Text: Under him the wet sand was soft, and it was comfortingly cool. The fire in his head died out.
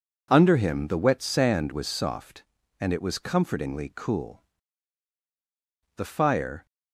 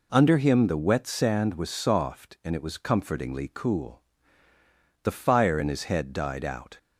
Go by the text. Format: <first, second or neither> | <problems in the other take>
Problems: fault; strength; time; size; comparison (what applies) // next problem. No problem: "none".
second | stops before "in his head died out"; at 6.6 s